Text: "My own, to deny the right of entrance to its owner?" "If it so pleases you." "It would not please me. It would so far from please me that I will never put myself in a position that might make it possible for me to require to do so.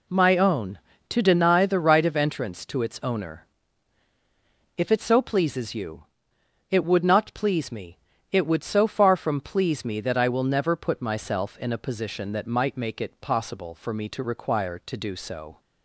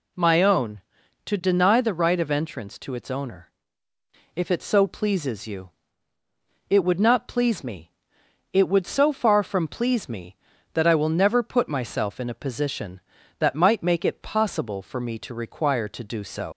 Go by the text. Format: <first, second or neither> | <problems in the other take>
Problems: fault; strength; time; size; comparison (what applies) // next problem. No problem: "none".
first | leaves "so" unfinished; at 16.5 s; 115 ms